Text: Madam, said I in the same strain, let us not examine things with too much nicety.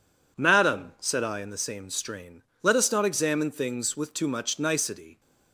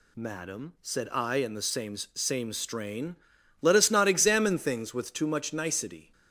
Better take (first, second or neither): first